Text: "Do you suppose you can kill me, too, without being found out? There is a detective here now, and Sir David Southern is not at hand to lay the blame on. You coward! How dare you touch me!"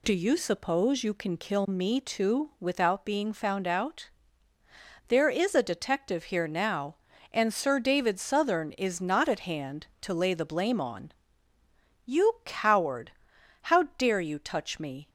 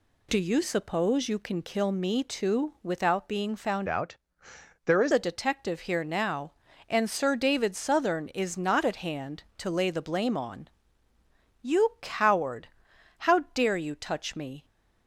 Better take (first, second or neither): first